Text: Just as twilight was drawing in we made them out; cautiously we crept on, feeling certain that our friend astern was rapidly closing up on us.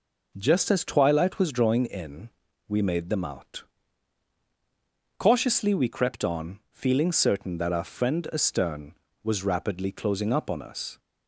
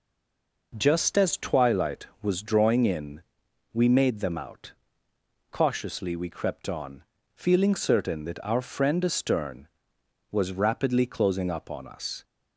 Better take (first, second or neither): first